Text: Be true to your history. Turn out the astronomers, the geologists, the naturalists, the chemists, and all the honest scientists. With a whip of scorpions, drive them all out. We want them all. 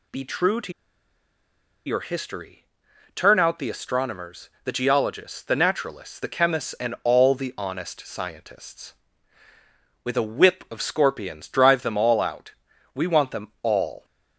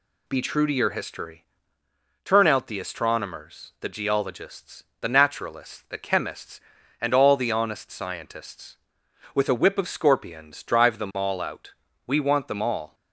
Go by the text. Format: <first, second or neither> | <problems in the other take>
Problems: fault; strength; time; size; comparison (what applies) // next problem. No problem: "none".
second | pauses between "to" and "your"; at 0.7 s; 1.1 s long